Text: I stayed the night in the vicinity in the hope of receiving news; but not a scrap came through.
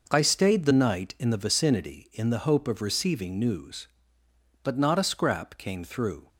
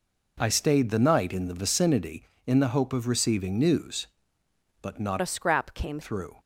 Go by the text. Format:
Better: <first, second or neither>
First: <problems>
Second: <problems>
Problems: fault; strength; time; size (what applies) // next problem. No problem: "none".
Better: first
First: none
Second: changes voice from "a" to "came"; from 5.2 to 6.0 s; 0.8 s long